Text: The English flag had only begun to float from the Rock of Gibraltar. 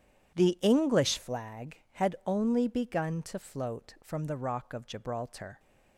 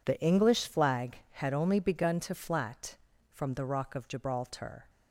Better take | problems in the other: first | says "flat" for "float"; at 2.3 s

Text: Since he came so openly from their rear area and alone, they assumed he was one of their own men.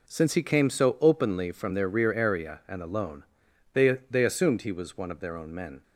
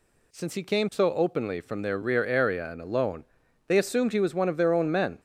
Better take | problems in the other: second | says "they" twice; at 4.1 s

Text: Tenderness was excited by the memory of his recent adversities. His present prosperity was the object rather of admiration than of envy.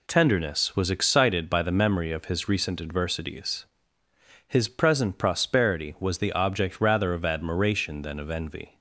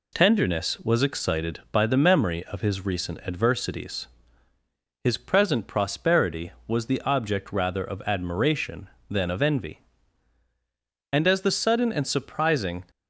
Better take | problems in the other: first | goes on to say "And as the sudden and surprising"; strong; from 11.1 s on; 1.7 s long

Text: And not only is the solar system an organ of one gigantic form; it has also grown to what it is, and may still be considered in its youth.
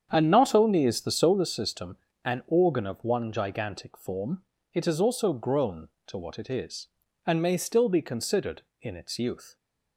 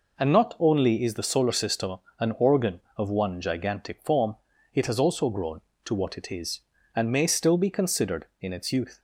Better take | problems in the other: second | starts louder than the rest; strong; until 1.5 s; 8 dB // pauses between "system" and "an"; slight; at 1.9 s; 0.28 s long; slight in the second

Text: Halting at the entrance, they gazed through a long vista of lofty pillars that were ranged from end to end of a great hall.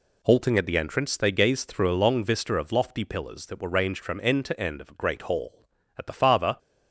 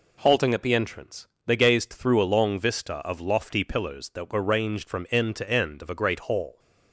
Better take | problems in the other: second | goes on to say "At the farther"; from 5.9 s on; 0.60 s long

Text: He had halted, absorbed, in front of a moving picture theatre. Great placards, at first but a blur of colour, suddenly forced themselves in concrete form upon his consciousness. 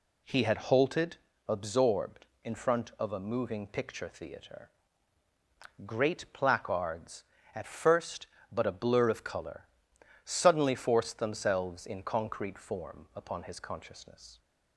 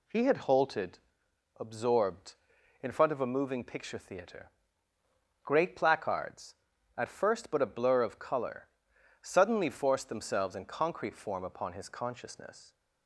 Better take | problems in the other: neither | none

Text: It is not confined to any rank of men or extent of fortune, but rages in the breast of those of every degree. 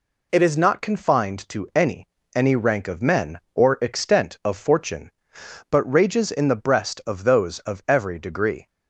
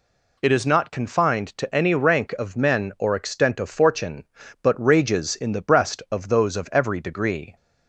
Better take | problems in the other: second | says "any" twice; at 2.3 s

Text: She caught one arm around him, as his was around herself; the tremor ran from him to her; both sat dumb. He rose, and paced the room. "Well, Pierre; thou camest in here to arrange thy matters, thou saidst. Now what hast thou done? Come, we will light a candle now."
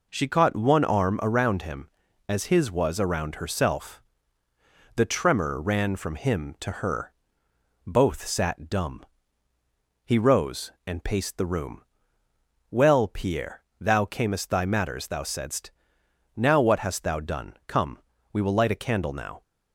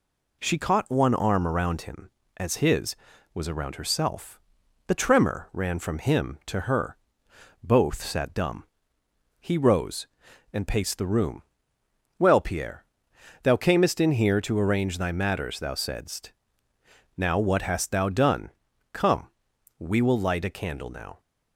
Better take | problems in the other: second | skips "in here to arrange"; at 14.4 s

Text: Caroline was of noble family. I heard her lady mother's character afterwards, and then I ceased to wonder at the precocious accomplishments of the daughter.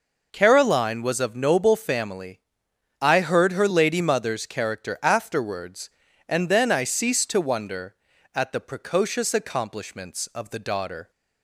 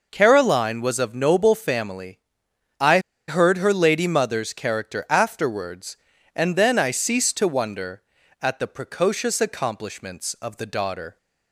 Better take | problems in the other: first | pauses between "I" and "heard"; slight; at 2.9 s; 0.29 s long

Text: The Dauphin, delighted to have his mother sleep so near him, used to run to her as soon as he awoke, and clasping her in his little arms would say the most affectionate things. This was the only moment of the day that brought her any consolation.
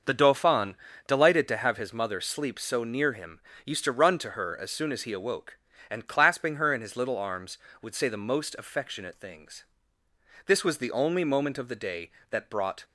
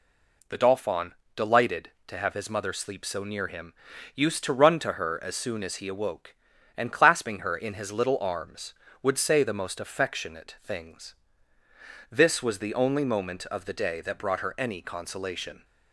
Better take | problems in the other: second | starts louder than the rest; until 1.3 s; 6 dB // stops before "her any consolation"; at 12.8 s

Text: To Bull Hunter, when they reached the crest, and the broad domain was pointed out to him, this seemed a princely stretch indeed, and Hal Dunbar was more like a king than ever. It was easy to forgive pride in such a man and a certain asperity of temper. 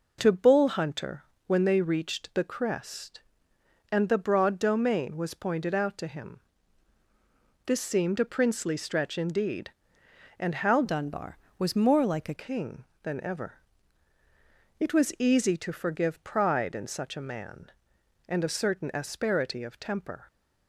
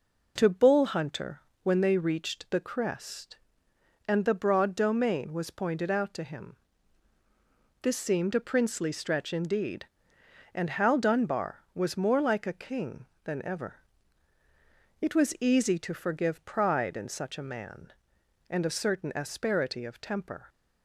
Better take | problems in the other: second | changes voice from "Dunbar" to "a"; from 10.8 to 12.3 s; 1.5 s long

